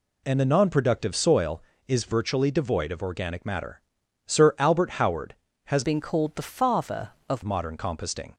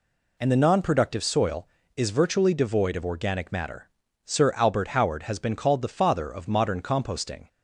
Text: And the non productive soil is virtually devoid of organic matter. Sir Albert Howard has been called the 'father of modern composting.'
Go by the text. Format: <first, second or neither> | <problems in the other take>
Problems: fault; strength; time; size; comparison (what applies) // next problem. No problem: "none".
second | changes voice from "been" to "of"; from 5.8 to 7.4 s; 1.6 s long